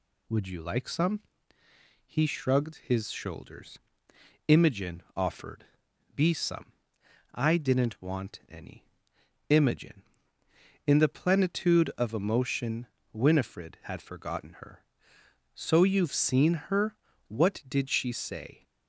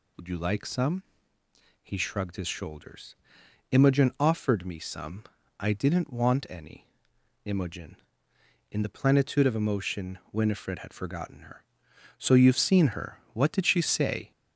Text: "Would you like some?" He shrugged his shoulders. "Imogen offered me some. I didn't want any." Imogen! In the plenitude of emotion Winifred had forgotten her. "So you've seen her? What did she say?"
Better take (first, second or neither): second